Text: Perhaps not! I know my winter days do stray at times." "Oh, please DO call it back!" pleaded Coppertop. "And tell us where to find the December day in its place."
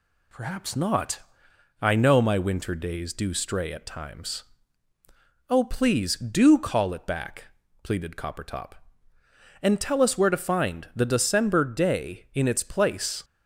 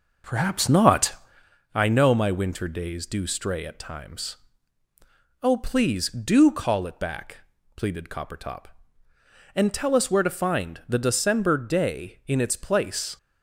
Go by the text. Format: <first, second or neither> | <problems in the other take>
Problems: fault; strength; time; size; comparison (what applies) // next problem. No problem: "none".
first | starts louder than the rest; noticeable; until 1.5 s; 6 dB